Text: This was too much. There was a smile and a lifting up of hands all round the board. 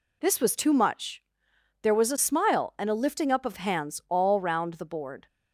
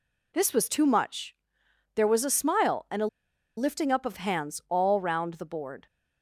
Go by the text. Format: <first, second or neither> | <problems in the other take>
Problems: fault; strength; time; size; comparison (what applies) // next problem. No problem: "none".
first | pauses between "a" and "lifting"; noticeable; at 3.0 s; 0.50 s long